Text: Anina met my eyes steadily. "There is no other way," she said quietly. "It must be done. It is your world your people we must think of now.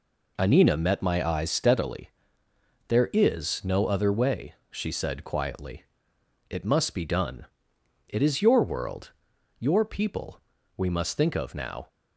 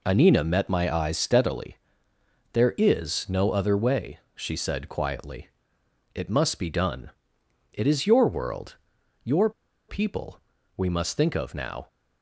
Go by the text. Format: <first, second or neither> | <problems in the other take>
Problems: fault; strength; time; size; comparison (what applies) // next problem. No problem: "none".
first | pauses between "world" and "your"; noticeable; at 8.7 s; 0.46 s long; noticeable in the first // pauses between "your" and "people"; at 9.5 s; 0.38 s long // pauses between "people" and "we"; at 10.3 s; 0.38 s long; also in the first